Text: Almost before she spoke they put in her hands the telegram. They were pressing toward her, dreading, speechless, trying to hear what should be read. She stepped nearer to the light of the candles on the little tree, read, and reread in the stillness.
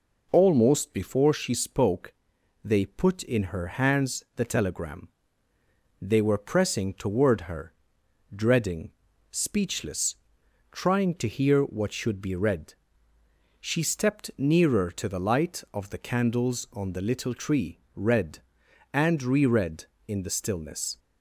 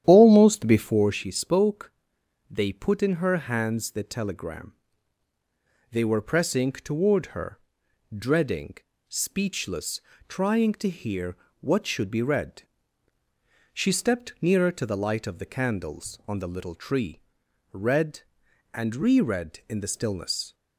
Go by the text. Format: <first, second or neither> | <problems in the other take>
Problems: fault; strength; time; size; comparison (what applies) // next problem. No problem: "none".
first | starts louder than the rest; strong; until 1.2 s; 10.5 dB // pauses between "spoke" and "they"; noticeable; at 1.9 s; 0.60 s long; noticeable in the first // pauses between "hear" and "what"; slight; at 11.3 s; 0.24 s long